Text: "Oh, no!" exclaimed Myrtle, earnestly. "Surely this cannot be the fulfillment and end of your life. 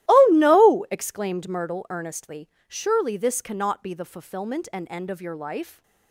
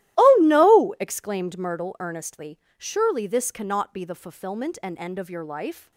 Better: neither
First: starts louder than the rest; strong; until 1.1 s; 15.5 dB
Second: starts louder than the rest; strong; until 1.2 s; 15 dB

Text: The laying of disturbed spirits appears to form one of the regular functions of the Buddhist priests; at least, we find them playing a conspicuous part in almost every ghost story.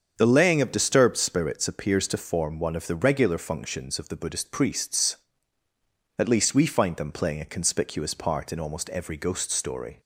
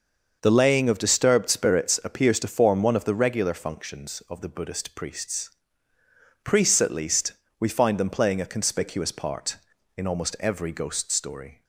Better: first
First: starts louder than the rest; until 1.1 s; 7 dB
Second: starts louder than the rest; noticeable; until 1.4 s; 6 dB // says "priests" twice; at 6.4 s

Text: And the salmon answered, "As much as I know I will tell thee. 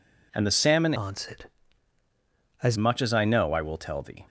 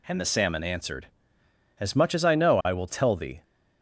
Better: second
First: changes voice from "answered" to "As"; from 0.9 to 2.7 s; 1.8 s long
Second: none

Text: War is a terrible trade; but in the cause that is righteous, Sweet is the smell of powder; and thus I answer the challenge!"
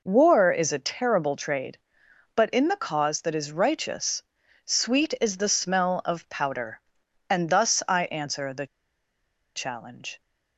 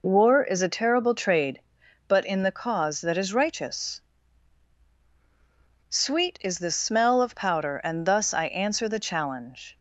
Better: second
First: pauses between "the" and "challenge"; noticeable; at 8.6 s; 0.89 s long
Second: none

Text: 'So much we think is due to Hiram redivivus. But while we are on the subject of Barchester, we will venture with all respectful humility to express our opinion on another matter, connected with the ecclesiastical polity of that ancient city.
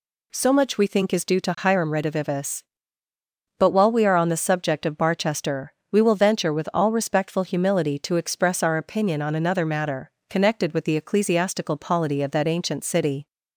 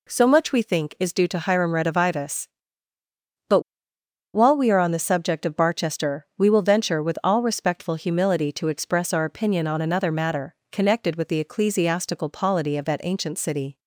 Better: first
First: none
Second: pauses between "But" and "while"; noticeable; at 3.5 s; 0.74 s long

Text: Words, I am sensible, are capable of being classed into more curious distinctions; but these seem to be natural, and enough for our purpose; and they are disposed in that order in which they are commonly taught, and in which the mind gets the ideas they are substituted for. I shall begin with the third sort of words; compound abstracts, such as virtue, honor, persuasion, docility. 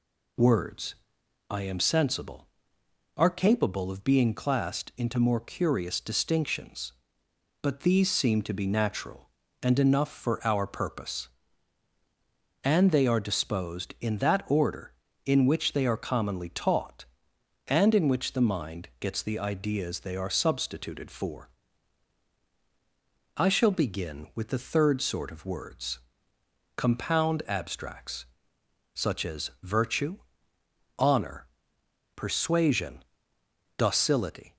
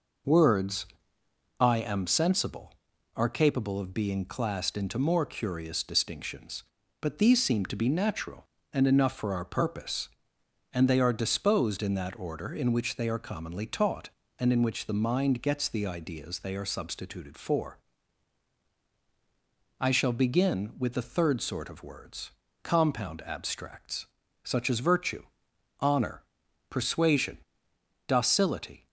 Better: neither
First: none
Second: none

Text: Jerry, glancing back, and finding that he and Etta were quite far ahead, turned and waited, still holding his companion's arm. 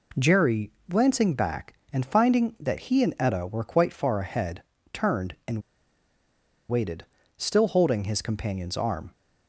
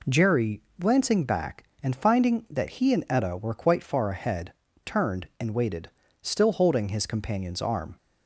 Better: second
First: pauses between "and" and "waited"; at 5.6 s; 1.0 s long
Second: none

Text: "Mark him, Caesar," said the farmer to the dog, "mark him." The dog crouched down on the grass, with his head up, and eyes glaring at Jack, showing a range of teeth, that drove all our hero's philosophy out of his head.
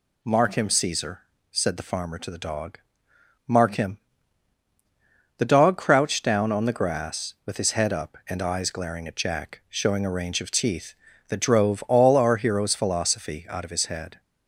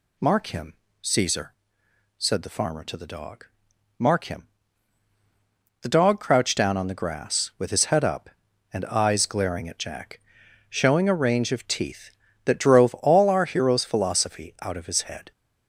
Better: neither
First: none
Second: none

